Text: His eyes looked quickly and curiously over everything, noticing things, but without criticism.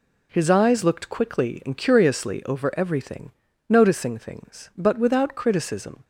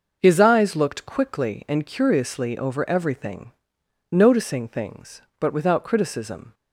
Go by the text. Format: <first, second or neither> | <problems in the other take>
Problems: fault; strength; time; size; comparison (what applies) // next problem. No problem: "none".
neither | none